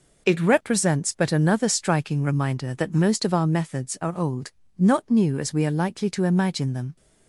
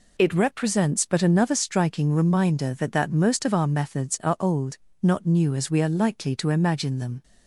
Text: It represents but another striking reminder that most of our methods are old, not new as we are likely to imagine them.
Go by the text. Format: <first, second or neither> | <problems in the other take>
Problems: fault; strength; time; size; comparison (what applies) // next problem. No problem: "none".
first | says "that" twice; at 2.9 s